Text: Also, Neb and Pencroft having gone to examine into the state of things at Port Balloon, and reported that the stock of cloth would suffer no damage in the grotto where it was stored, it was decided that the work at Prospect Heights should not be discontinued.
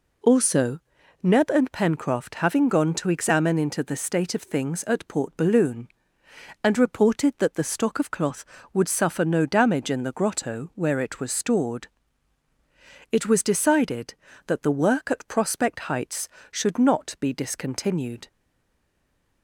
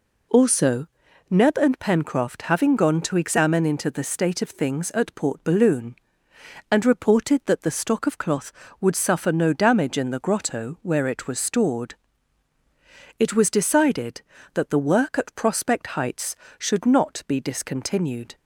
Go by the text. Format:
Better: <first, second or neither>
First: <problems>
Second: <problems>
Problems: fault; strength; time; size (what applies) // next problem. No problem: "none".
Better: second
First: stays silent after the last word; from 18.2 s on; 1.2 s long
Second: none